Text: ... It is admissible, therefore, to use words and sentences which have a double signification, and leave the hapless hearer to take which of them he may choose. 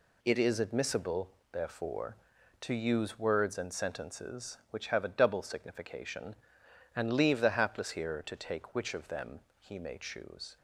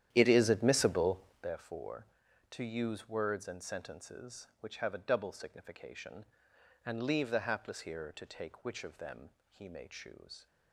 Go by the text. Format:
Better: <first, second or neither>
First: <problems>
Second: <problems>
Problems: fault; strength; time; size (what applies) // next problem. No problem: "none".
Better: first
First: pauses between "them" and "he"; slight; at 9.3 s; 0.22 s long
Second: starts louder than the rest; strong; until 1.5 s; 11 dB // pauses between "them" and "he"; slight; at 9.2 s; 0.22 s long